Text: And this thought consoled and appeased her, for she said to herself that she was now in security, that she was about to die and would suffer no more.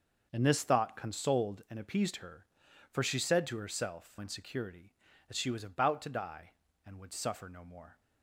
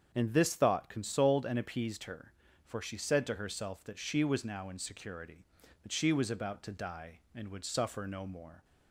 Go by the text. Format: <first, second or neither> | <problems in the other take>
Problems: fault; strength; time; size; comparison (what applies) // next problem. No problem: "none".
second | starts louder than the rest; until 1.3 s; 6.5 dB; strong in the second // skips "that she was now"; at 4.1 s